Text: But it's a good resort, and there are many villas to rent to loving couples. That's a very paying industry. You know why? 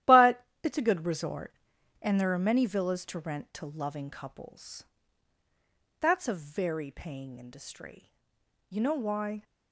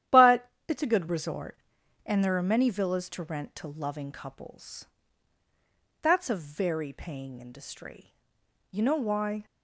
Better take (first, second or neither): second